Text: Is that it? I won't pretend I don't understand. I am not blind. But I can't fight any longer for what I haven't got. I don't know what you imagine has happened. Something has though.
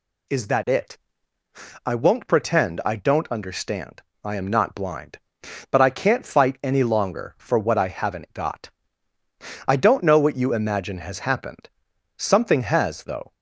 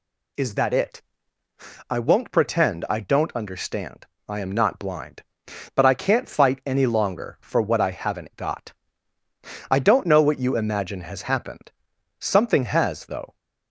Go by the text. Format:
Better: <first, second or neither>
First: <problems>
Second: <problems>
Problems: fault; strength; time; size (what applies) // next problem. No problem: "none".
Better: neither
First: none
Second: none